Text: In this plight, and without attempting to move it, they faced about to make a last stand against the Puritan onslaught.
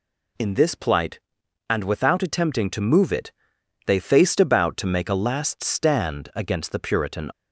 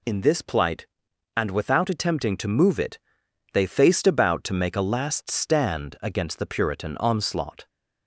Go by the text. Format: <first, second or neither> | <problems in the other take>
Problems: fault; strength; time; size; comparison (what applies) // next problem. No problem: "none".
second | stops before "onslaught"; at 7.3 s